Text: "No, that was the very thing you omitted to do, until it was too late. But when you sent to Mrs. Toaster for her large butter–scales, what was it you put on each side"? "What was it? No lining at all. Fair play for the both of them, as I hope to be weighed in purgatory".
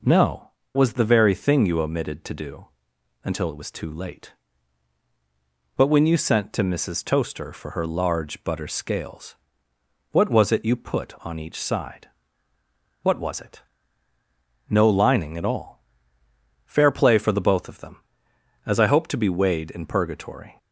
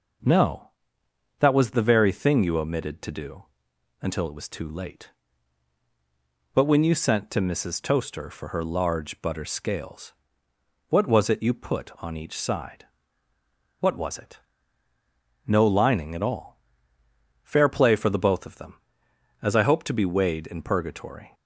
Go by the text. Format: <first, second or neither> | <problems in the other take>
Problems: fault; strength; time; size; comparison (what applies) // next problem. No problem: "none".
second | skips "that"; at 0.6 s